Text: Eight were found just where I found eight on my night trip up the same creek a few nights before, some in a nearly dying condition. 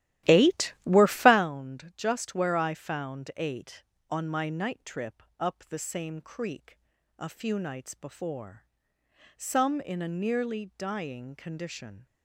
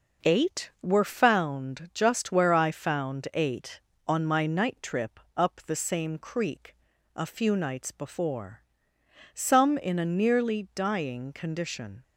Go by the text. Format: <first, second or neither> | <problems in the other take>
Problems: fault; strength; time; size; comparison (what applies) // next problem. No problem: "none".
second | starts louder than the rest; strong; until 1.5 s; 14 dB // pauses between "trip" and "up"; slight; at 5.2 s; 0.16 s long; slight in the second // pauses between "creek" and "a"; at 6.7 s; 0.42 s long; also in the second